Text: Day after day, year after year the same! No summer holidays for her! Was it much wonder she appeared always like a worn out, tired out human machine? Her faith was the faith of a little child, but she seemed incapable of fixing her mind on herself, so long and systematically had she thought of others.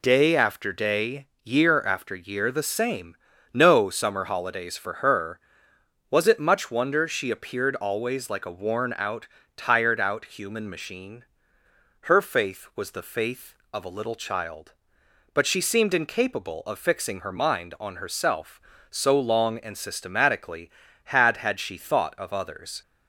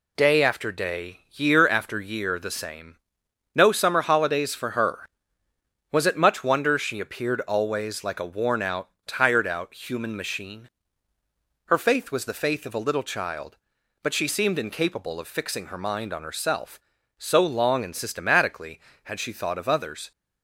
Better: second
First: says "had" twice; at 21.3 s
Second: none

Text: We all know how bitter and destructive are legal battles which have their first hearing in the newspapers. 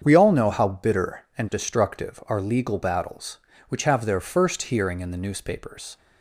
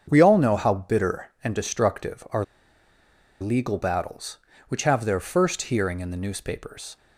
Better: first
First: starts louder than the rest; strong; until 1.0 s; 7.5 dB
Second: starts louder than the rest; strong; until 1.1 s; 7.5 dB // pauses between "are" and "legal"; noticeable; at 2.4 s; 0.98 s long

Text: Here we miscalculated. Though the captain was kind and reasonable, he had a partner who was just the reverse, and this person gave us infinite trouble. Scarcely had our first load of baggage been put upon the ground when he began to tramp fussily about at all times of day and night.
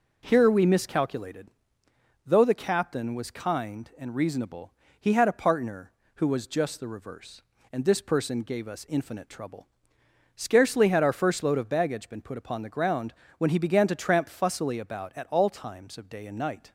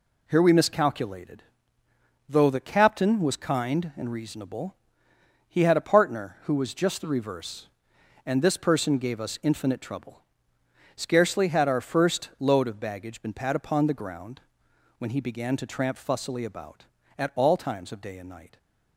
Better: first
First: pauses between "ground" and "when"; slight; at 13.1 s; 0.24 s long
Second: says "pat" for "put"; at 13.3 s // pauses between "ground" and "when"; noticeable; at 14.3 s; 0.58 s long

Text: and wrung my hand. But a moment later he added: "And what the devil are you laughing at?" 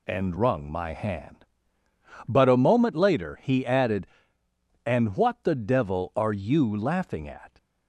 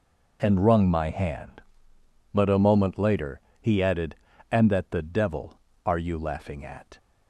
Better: first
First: none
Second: pauses between "later" and "he"; slight; at 3.4 s; 0.20 s long // says "that" for "what"; at 4.7 s

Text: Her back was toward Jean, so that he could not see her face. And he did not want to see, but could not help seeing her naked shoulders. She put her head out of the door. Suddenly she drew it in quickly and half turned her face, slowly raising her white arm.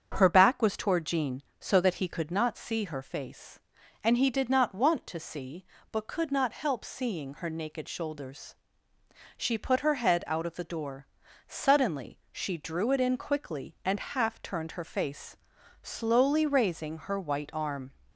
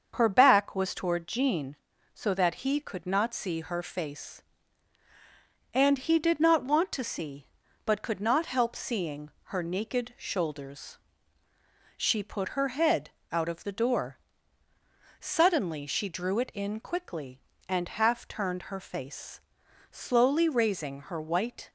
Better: first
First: starts louder than the rest; strong; until 1.1 s; 7.5 dB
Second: starts louder than the rest; until 1.1 s; 7 dB // pauses between "seeing" and "her"; slight; at 9.3 s; 0.16 s long // pauses between "head" and "out"; slight; at 13.1 s; 0.22 s long // stops before "arm"; at 21.6 s

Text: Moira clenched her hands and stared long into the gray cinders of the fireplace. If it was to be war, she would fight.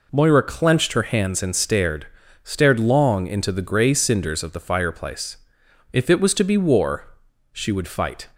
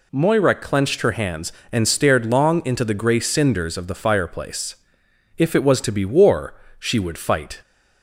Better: second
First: says "stared" twice; at 2.4 s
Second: none

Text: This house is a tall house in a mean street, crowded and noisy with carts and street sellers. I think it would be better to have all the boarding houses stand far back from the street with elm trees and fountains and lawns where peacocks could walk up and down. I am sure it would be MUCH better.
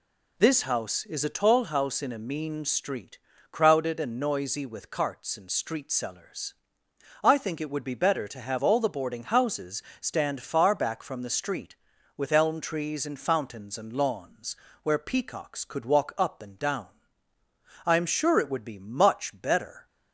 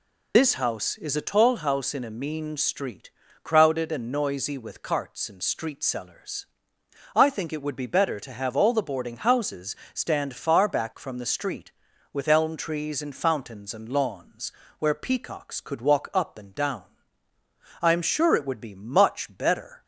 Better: first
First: pauses between "houses" and "stand"; slight; at 9.8 s; 0.20 s long // pauses between "lawns" and "where"; slight; at 14.5 s; 0.26 s long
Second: loses the start of "This"; at 0.3 s; 45 ms // pauses between "houses" and "stand"; slight; at 9.7 s; 0.20 s long // pauses between "lawns" and "where"; slight; at 14.5 s; 0.26 s long

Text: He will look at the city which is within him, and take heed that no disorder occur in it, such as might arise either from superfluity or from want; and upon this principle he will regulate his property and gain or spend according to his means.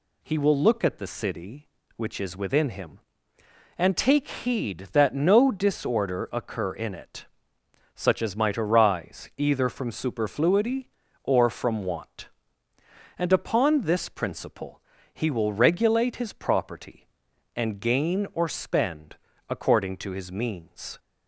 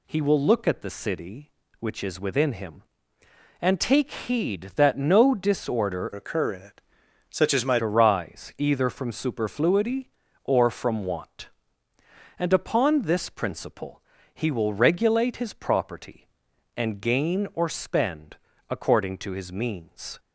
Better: first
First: pauses between "principle" and "he"; slight; at 14.8 s; 0.32 s long // pauses between "spend" and "according"; slight; at 19.1 s; 0.32 s long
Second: changes voice from "occur" to "might"; from 6.1 to 7.8 s; 1.7 s long // pauses between "principle" and "he"; slight; at 14.0 s; 0.32 s long // pauses between "spend" and "according"; slight; at 18.3 s; 0.32 s long

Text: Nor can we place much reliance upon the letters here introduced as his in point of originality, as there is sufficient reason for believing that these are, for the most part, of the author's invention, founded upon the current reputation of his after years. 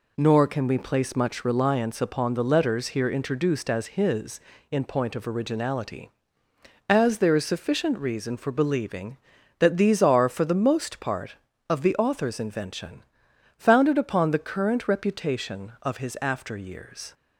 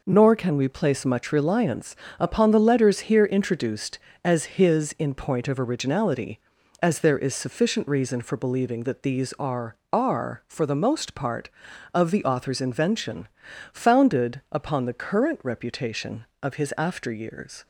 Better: first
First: none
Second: pauses between "reliance" and "upon"; slight; at 1.9 s; 0.24 s long // says "are" twice; at 9.9 s

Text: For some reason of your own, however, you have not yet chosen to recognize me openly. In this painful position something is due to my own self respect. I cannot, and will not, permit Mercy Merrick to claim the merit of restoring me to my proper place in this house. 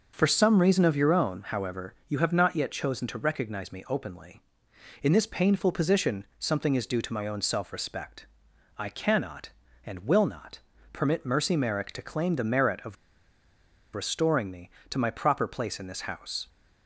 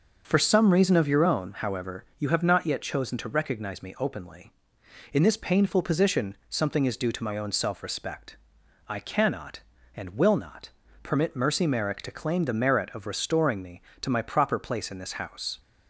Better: second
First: starts louder than the rest; until 1.1 s; 6.5 dB // pauses between "of" and "restoring"; at 12.9 s; 0.98 s long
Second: starts louder than the rest; until 1.2 s; 6.5 dB

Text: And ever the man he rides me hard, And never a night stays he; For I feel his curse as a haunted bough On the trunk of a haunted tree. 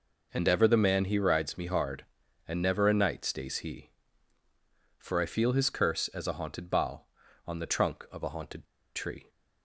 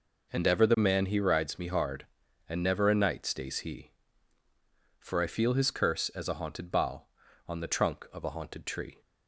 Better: second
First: pauses between "haunted" and "tree"; slight; at 8.6 s; 0.32 s long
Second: none

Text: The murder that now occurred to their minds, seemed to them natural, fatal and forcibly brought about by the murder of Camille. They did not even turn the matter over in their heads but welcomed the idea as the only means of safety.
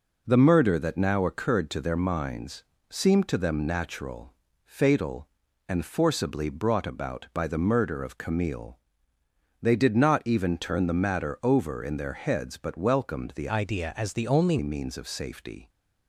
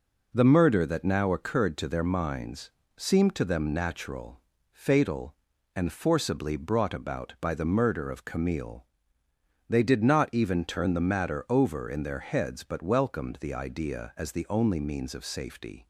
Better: second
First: changes voice from "idea" to "only"; from 13.4 to 14.5 s; 1.1 s long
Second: none

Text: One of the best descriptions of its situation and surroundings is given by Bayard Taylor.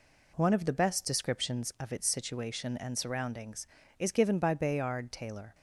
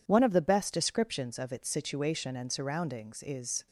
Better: first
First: none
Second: stops before "given by Bayard Taylor"; at 3.6 s

